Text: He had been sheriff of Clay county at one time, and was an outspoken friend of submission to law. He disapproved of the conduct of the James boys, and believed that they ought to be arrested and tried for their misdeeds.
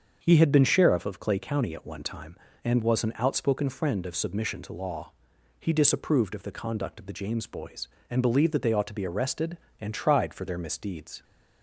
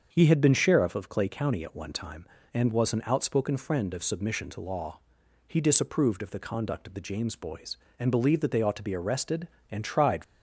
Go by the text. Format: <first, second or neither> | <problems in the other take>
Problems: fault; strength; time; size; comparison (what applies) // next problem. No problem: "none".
first | starts louder than the rest; until 1.1 s; 7 dB; also in the first // stops before "for their misdeeds"; at 10.2 s